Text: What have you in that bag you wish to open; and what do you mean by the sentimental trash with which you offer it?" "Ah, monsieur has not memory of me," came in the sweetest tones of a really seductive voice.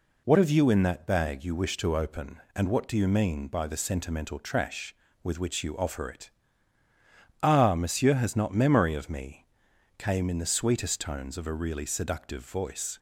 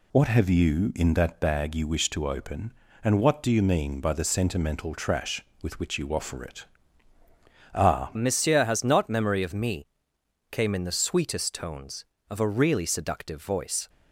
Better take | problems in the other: first | changes voice at "monsieur"; from 8.1 s on; 5.7 s long

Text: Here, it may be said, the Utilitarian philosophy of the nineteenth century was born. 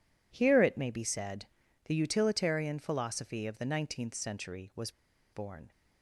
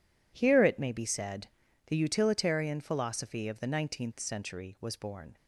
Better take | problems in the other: second | pauses between "was" and "born"; at 4.9 s; 0.42 s long

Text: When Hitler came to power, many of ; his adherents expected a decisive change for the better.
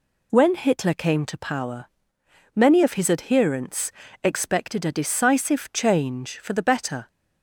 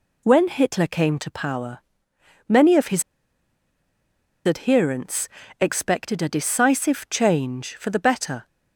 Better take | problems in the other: first | pauses between "his" and "adherents"; strong; at 3.0 s; 1.4 s long // pauses between "adherents" and "expected"; slight; at 5.2 s; 0.32 s long; slight in the first

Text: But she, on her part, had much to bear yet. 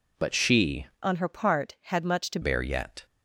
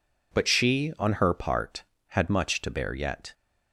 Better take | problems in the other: second | changes voice from "on" to "to"; from 1.0 to 2.3 s; 1.3 s long

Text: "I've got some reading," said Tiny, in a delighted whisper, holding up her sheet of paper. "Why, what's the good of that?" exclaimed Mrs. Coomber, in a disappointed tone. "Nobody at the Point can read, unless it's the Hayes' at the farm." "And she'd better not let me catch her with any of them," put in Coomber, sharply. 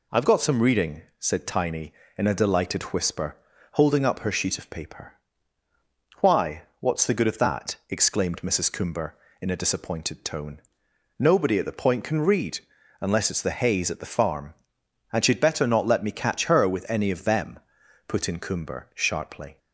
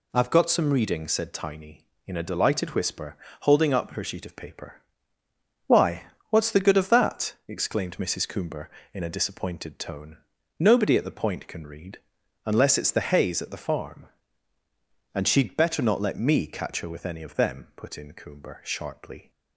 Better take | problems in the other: neither | none

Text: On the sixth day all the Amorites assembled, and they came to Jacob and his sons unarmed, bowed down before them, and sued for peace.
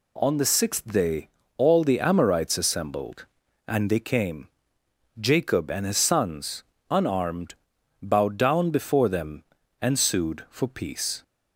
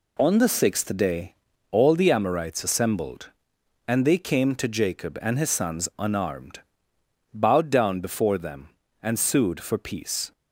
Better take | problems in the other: second | pauses between "day" and "all"; slight; at 1.2 s; 0.30 s long; slight in the second // skips "to"; at 4.8 s // pauses between "sons" and "unarmed"; slight; at 6.6 s; 0.26 s long

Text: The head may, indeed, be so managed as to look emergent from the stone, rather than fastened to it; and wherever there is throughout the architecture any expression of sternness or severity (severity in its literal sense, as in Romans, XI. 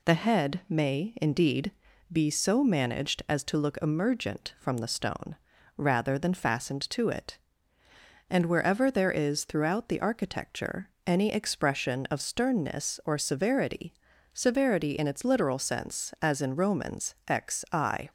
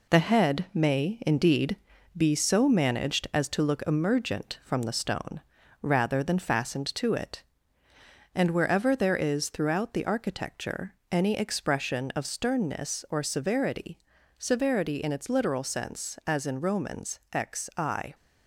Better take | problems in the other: first | gets quieter; noticeable; throughout; 5 dB // pauses between "architecture" and "any"; slight; at 10.9 s; 0.16 s long; slight in the first

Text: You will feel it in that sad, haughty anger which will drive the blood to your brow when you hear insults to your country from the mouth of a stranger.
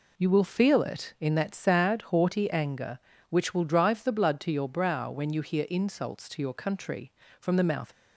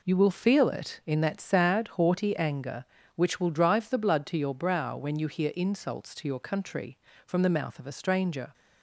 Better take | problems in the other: second | stops before "of a stranger"; at 7.9 s

